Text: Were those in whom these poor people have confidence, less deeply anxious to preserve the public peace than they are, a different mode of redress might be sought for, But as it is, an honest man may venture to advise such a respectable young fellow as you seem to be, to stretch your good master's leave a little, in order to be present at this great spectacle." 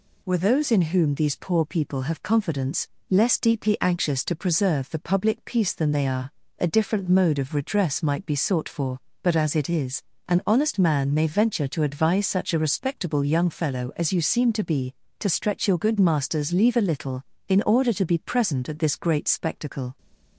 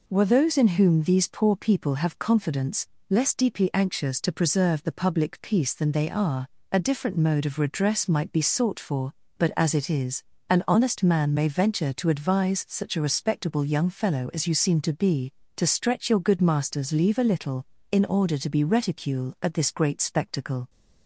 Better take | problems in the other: first | says "reticule" for "present"; at 18.6 s

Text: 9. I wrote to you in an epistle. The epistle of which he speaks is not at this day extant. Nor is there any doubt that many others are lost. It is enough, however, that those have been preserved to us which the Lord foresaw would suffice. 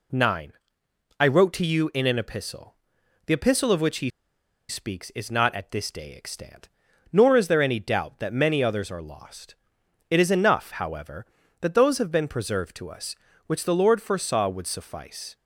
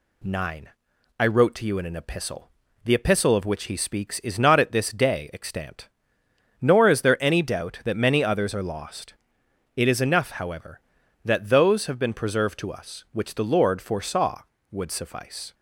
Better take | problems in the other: second | pauses between "he" and "speaks"; noticeable; at 4.0 s; 0.59 s long

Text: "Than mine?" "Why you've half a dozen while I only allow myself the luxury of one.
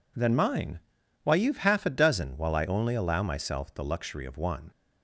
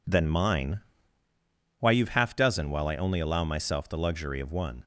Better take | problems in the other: first | skips "a"; at 2.3 s

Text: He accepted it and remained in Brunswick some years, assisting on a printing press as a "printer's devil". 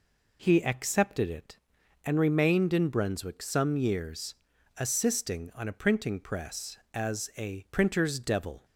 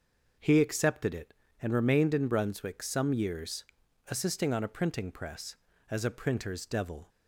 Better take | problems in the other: neither | none

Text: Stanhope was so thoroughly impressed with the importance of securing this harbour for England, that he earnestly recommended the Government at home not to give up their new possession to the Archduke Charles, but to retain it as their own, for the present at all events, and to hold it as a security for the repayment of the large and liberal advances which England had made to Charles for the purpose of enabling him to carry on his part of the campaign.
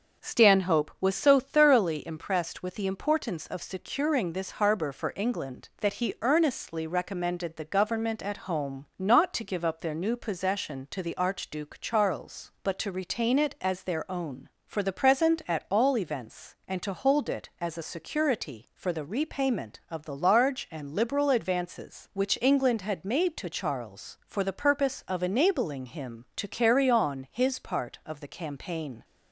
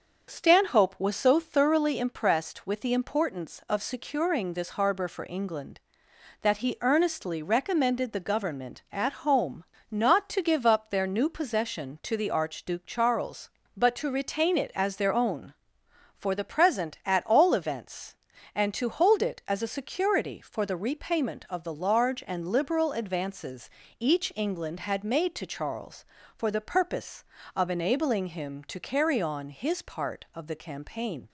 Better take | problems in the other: first | starts louder than the rest; until 1.3 s; 6.5 dB; also in the first // pauses between "home" and "not"; slight; at 9.6 s; 0.26 s long // says "each" for "which"; at 23.9 s

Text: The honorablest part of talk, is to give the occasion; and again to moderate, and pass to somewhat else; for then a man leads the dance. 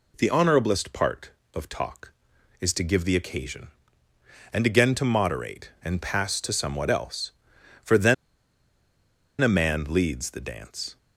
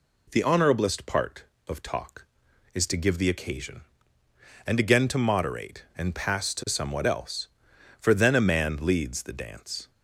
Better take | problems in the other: second | pauses between "then" and "a"; strong; at 8.1 s; 1.2 s long

